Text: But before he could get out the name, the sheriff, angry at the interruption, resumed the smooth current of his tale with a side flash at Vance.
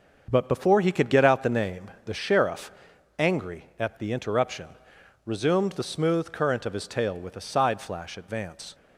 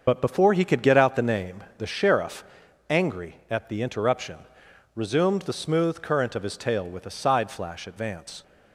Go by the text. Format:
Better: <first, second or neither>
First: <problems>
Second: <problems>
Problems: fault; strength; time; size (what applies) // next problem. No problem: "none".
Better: first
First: starts louder than the rest; until 1.3 s; 6.5 dB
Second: loses the start of "But"; at 0.0 s; 65 ms // starts louder than the rest; until 1.0 s; 6.5 dB